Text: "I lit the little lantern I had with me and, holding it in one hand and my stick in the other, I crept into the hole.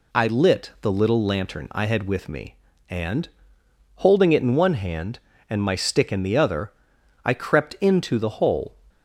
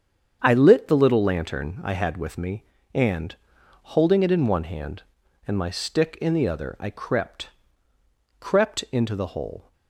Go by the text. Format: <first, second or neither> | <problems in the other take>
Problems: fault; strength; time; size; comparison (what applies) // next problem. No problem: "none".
first | starts louder than the rest; strong; until 1.4 s; 7.5 dB // says "crept" twice; at 8.3 s